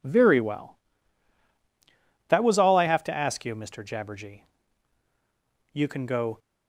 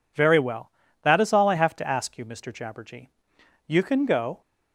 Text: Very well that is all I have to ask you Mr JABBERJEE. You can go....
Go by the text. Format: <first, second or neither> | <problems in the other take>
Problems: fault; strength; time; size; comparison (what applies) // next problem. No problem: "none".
second | says "was" for "is"; at 2.4 s